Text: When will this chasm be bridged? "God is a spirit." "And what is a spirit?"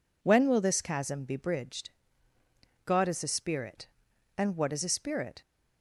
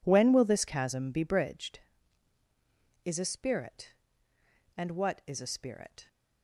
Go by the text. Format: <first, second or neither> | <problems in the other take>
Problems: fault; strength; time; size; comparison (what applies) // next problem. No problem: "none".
first | skips "God"; at 2.4 s